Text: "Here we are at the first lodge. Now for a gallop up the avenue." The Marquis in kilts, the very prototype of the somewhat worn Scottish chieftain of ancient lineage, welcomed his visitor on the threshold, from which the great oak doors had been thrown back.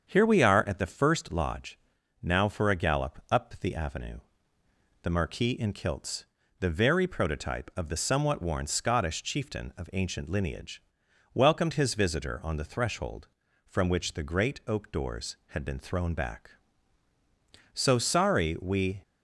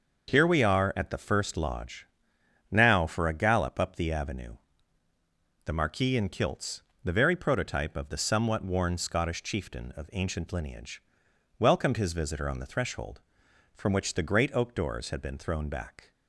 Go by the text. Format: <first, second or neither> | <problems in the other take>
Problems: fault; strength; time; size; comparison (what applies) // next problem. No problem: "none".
second | starts louder than the rest; strong; until 1.1 s; 7.5 dB // goes on to say "So sorry we"; noticeable; from 17.7 s on; 1.2 s long